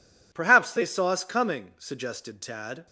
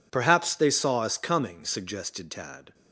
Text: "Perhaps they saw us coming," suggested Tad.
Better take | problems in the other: neither | none

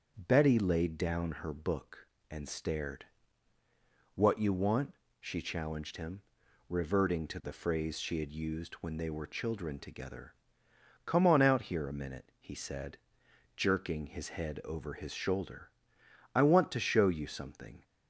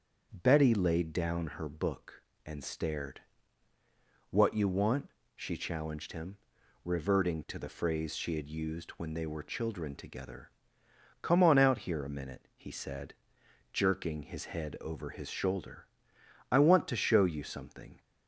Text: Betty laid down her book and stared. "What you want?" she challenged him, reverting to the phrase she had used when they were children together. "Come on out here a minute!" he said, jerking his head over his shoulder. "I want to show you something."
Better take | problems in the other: neither | starts louder than the rest; the same in both

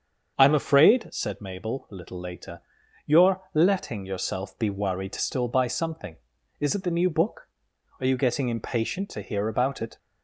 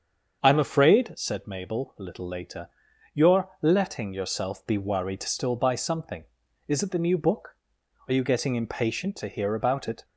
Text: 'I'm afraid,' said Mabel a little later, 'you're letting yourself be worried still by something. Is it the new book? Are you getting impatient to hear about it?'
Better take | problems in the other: neither | starts louder than the rest; the same in both

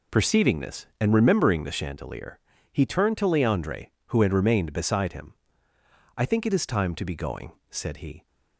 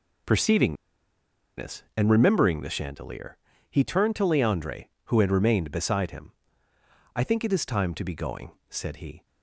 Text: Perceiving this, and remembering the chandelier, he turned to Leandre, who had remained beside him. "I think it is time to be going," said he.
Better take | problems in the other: first | pauses between "Perceiving" and "this"; noticeable; at 0.7 s; 0.83 s long

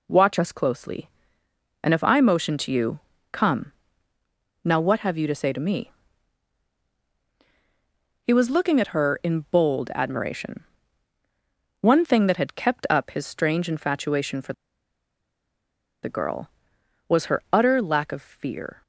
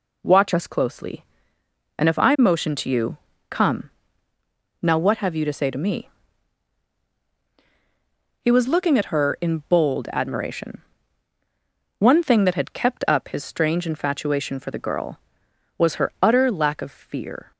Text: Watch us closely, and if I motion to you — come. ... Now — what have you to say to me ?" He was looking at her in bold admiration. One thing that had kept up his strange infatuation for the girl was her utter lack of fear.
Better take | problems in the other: second | pauses between "for" and "the"; strong; at 14.5 s; 1.4 s long

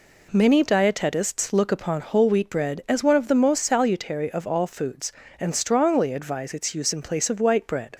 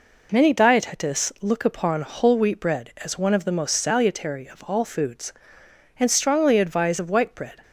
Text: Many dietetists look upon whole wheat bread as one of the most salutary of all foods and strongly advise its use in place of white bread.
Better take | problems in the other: first | skips "its use in place"; at 6.9 s

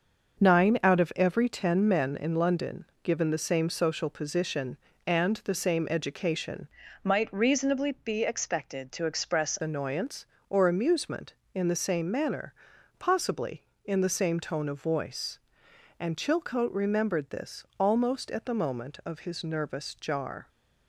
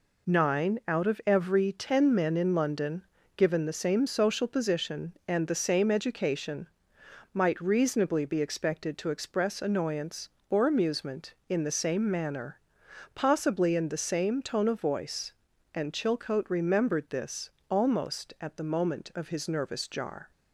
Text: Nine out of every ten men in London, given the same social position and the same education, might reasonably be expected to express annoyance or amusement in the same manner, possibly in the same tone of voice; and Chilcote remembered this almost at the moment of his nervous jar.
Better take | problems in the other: second | starts louder than the rest; until 1.4 s; 6 dB // changes voice from "might" to "express"; from 7.0 to 9.5 s; 2.5 s long // pauses between "this" and "almost"; slight; at 17.6 s; 0.16 s long; slight in the second

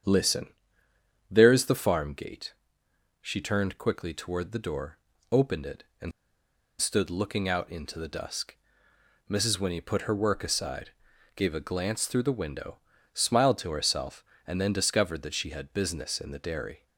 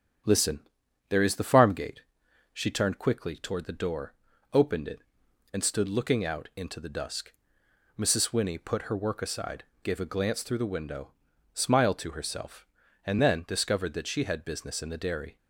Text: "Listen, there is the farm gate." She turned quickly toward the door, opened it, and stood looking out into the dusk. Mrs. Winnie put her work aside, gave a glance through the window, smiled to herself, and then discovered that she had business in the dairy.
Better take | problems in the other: second | starts louder than the rest; strong; until 1.8 s; 8 dB; strong in the second // pauses between "and" and "stood"; noticeable; at 6.1 s; 0.69 s long

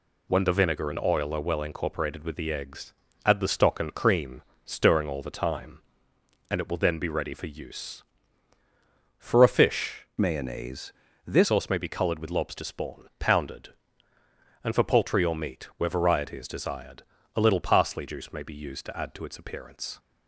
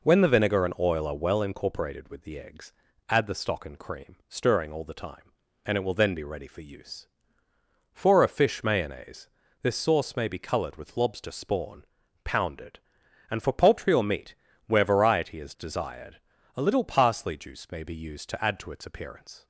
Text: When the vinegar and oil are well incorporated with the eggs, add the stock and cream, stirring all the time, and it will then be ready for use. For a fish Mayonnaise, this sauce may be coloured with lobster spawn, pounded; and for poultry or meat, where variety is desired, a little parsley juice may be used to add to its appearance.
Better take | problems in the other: second | changes voice from "Mayonnaise" to "this"; from 10.2 to 11.4 s; 1.2 s long

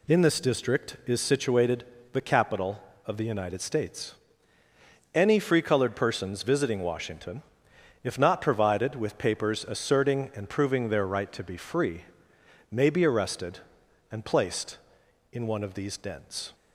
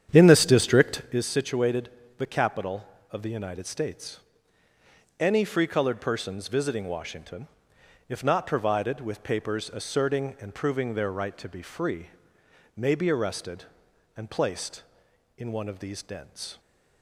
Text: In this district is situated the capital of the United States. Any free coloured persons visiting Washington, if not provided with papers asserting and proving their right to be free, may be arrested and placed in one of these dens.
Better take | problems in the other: first | starts louder than the rest; strong; until 1.3 s; 9 dB // pauses between "situated" and "the"; slight; at 1.8 s; 0.30 s long; slight in the first

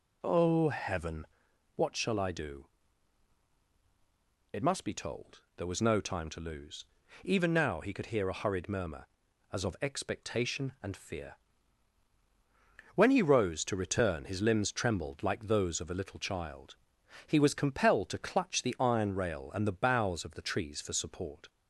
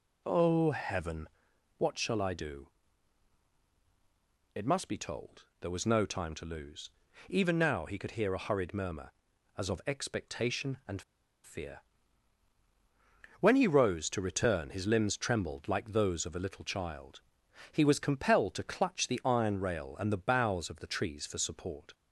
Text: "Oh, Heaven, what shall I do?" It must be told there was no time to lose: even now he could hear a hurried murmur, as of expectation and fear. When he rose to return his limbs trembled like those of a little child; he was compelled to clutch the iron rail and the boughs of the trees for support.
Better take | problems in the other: first | pauses between "told" and "there"; slight; at 5.4 s; 0.16 s long; slight in the first // pauses between "and" and "fear"; at 11.0 s; 0.43 s long

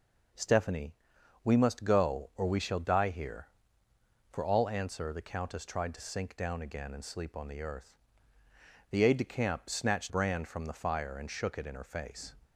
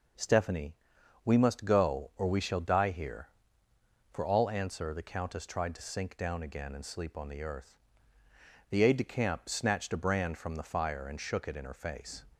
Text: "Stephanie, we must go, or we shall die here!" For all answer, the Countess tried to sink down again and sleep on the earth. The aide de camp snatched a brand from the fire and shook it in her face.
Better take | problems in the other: second | skips "a"; at 10.0 s

